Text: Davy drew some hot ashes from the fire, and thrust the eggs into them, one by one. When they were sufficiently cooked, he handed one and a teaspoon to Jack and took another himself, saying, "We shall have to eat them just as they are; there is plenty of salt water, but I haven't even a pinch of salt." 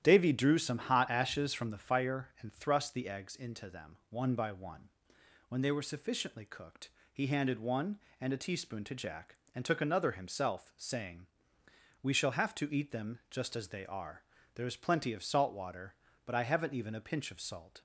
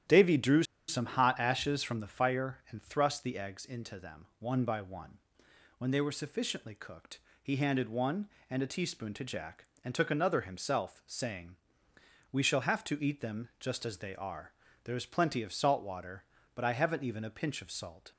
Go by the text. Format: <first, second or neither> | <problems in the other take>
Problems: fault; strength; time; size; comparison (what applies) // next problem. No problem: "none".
first | starts louder than the rest; strong; until 1.3 s; 11 dB; strong in the first // pauses between "drew" and "some"; slight; at 0.6 s; 0.25 s long